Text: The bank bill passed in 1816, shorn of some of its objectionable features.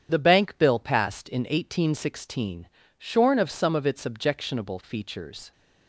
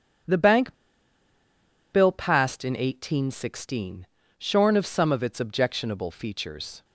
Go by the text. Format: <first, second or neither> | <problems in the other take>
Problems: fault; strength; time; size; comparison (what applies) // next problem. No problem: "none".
first | starts louder than the rest; strong; until 2.4 s; 8.5 dB; strong in the first // pauses between "bank" and "bill"; at 0.7 s; 1.1 s long